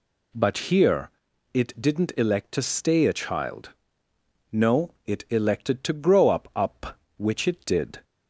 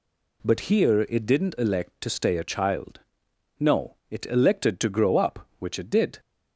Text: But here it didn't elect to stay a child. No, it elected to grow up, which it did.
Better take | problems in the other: second | pauses between "here" and "it"; at 1.1 s; 0.42 s long // says "up" twice; at 6.5 s

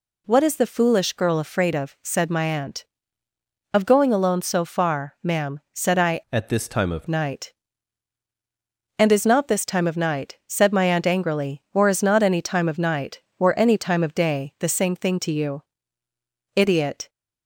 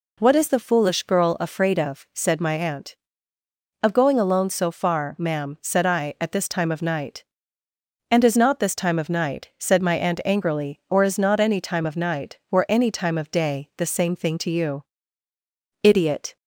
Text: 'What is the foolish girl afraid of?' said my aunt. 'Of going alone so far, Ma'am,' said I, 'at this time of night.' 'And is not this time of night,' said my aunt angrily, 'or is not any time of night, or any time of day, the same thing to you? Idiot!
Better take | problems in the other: second | changes voice from "at" to "of"; from 6.3 to 7.0 s; 0.7 s long

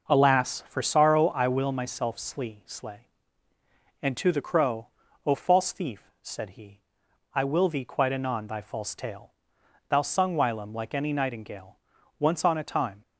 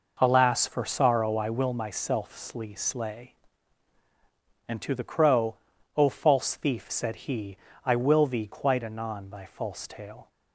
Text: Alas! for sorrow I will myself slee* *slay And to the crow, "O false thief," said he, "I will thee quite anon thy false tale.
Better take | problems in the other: second | goes on to say "Thou sung whilom like any nightingale once on a time"; strong; from 9.8 s on; 3.1 s long

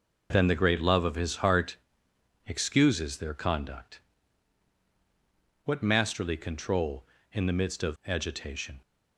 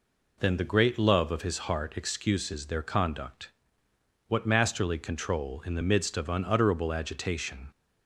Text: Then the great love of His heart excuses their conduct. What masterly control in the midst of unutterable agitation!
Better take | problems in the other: second | pauses between "heart" and "excuses"; noticeable; at 1.7 s; 0.72 s long // skips "unutterable"; at 8.0 s

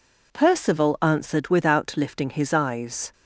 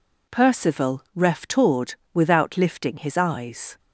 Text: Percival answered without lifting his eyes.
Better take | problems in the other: first | says "reftored" for "answered"; at 1.1 s

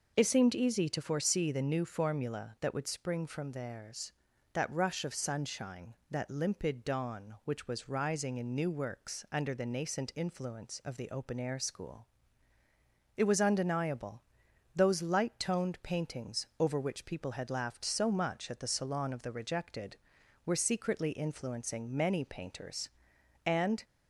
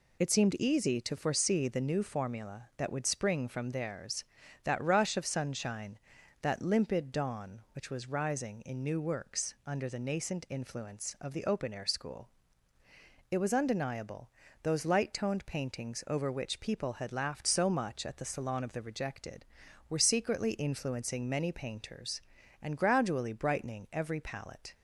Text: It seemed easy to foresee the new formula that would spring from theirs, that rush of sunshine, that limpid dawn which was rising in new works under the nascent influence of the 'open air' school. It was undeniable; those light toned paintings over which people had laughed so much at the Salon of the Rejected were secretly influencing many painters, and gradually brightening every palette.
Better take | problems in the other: second | stops before "gradually brightening every palette"; at 23.8 s

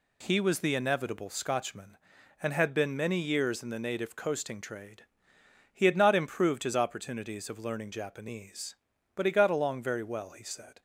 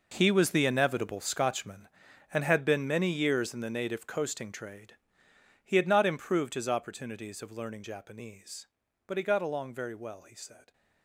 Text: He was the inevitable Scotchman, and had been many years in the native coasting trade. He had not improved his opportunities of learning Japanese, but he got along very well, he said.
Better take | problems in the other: first | gets quieter; strong; throughout; 14 dB

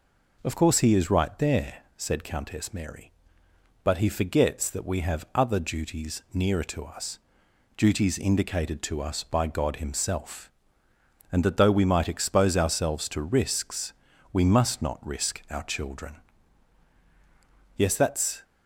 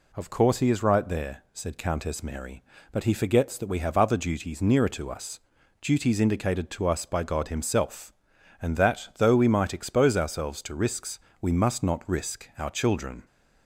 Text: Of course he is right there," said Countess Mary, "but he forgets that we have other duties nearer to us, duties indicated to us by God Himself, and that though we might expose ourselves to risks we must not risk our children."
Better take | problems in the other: second | pauses between "risks" and "we"; at 13.9 s; 0.40 s long; slight in the second // goes on to say "Yes that's"; noticeable; from 17.7 s on; 0.68 s long

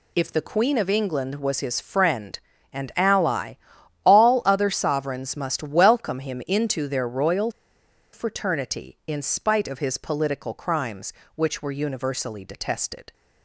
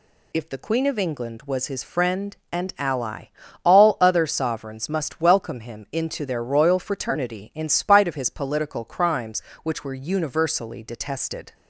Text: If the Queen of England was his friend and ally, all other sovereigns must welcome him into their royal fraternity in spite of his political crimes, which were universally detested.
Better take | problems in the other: second | pauses between "royal" and "fraternity"; noticeable; at 7.4 s; 0.63 s long

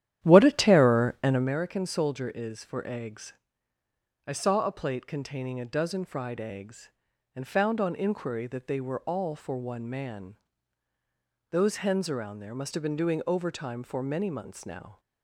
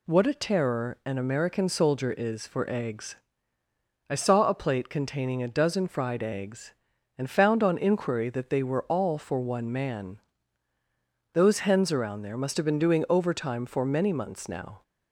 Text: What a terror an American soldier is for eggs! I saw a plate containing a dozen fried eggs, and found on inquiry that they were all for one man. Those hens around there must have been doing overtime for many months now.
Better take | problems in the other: second | starts louder than the rest; strong; until 1.6 s; 11 dB

